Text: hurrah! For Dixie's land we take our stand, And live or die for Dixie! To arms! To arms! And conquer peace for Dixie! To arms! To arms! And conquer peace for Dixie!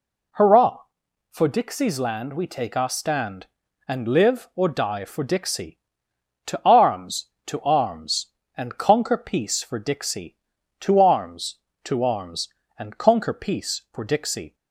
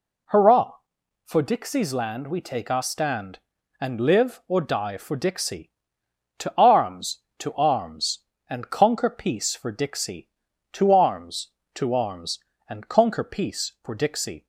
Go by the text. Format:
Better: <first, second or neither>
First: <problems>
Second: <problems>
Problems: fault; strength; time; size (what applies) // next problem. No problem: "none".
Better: neither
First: none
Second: none